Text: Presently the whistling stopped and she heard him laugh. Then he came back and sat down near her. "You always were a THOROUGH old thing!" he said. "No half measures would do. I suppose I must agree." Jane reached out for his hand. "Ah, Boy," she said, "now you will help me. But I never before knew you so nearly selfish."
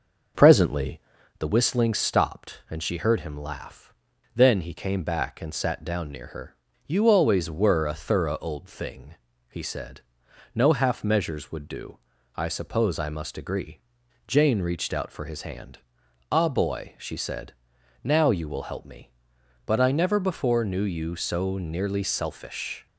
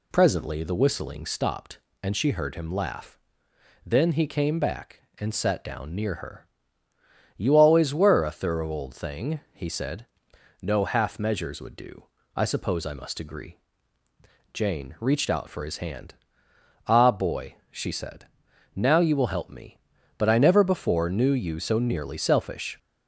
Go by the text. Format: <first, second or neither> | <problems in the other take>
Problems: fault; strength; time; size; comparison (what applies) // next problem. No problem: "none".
second | starts louder than the rest; noticeable; until 1.5 s; 6 dB // pauses between "Presently" and "the"; at 0.9 s; 0.38 s long